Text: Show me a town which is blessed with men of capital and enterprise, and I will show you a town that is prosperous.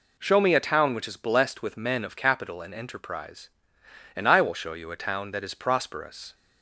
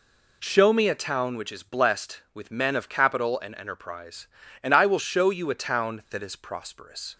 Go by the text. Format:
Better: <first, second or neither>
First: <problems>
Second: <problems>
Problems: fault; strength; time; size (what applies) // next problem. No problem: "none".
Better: neither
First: none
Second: none